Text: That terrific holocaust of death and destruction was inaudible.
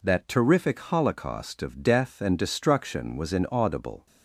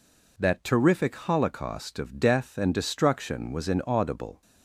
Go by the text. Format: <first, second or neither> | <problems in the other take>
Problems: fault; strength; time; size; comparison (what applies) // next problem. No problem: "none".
neither | none